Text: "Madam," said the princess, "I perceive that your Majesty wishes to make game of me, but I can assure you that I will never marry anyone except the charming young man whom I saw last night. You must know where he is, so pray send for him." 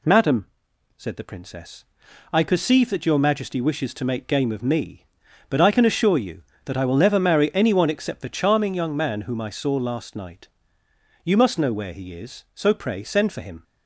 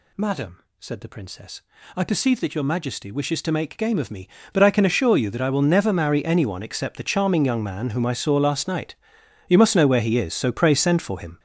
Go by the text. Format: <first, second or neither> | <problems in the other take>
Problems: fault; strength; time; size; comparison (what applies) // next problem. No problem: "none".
first | gets louder; strong; throughout; 10.5 dB